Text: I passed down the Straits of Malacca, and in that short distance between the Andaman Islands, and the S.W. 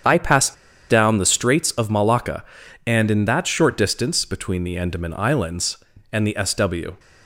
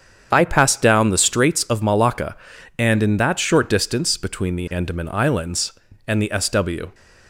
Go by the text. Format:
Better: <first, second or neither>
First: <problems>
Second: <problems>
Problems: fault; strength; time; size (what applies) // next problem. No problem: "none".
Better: second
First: starts louder than the rest; strong; until 1.4 s; 8 dB // pauses between "passed" and "down"; slight; at 0.5 s; 0.34 s long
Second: starts louder than the rest; strong; until 1.3 s; 8 dB